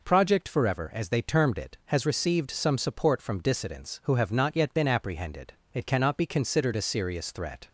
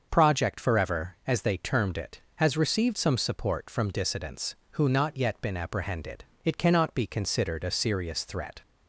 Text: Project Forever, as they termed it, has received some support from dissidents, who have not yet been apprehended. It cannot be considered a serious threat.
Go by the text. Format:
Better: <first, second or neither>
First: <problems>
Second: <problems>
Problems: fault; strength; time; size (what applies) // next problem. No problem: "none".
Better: first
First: none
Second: starts louder than the rest; until 1.1 s; 6.5 dB // skips "have"; at 4.8 s